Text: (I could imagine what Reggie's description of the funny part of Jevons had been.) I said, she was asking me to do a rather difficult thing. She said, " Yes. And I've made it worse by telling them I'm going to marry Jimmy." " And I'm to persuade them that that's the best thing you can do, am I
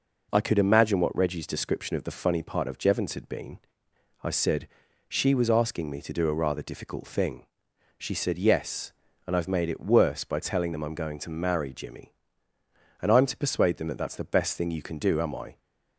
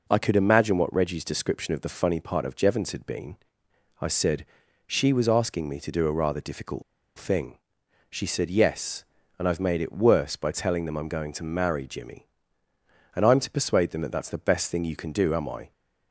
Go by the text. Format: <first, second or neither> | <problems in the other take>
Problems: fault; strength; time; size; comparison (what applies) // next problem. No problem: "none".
first | pauses between "difficult" and "thing"; slight; at 6.8 s; 0.35 s long